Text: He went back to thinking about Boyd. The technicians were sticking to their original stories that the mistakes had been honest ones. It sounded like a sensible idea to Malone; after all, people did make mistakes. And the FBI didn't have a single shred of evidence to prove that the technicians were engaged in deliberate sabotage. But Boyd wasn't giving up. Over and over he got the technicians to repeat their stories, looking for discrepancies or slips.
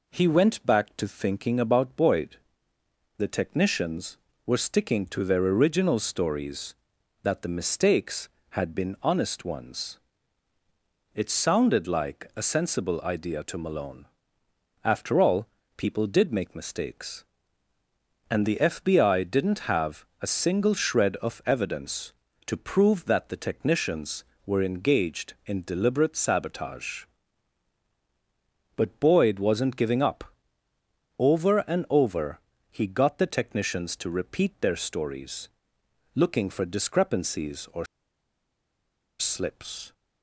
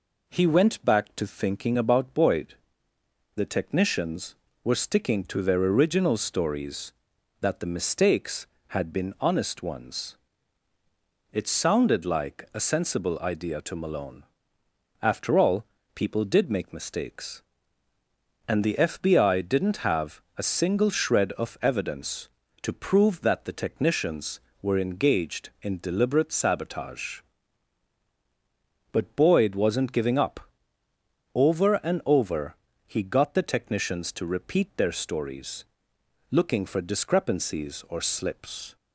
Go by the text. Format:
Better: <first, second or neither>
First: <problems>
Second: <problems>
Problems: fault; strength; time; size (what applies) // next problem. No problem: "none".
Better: second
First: pauses between "have" and "a"; slight; at 20.0 s; 0.16 s long // pauses between "over" and "he"; slight; at 32.3 s; 0.30 s long // pauses between "or" and "slips"; strong; at 37.8 s; 1.3 s long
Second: pauses between "have" and "a"; slight; at 20.2 s; 0.16 s long // pauses between "over" and "he"; slight; at 32.5 s; 0.30 s long